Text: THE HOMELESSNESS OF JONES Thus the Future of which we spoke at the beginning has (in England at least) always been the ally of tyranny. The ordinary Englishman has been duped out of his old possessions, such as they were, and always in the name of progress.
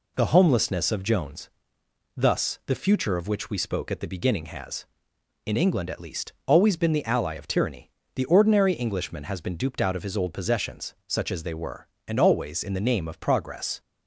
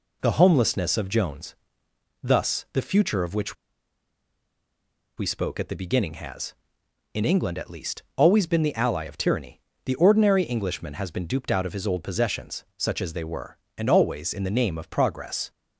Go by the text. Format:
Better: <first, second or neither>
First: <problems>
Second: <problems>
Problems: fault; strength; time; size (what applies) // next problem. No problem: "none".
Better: first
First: pauses between "JONES" and "Thus"; noticeable; at 1.4 s; 0.67 s long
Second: pauses between "JONES" and "Thus"; noticeable; at 1.5 s; 0.68 s long // pauses between "which" and "we"; strong; at 3.5 s; 1.6 s long